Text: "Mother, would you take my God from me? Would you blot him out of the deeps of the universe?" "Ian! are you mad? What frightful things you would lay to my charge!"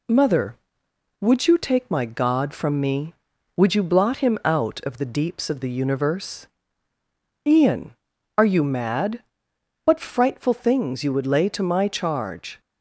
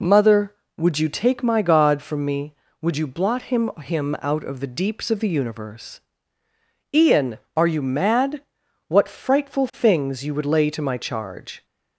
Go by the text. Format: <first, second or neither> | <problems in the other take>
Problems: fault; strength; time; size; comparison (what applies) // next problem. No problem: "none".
first | says "him" twice; at 3.7 s